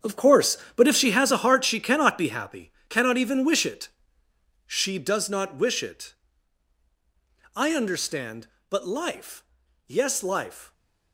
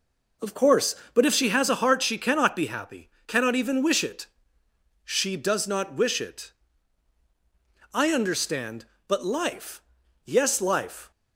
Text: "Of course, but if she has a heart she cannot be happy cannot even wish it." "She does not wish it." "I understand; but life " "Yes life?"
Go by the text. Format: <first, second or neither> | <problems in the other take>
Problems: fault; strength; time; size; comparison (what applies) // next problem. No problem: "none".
second | gets quieter; strong; throughout; 17 dB // pauses between "happy" and "cannot"; slight; at 2.7 s; 0.18 s long; slight in the second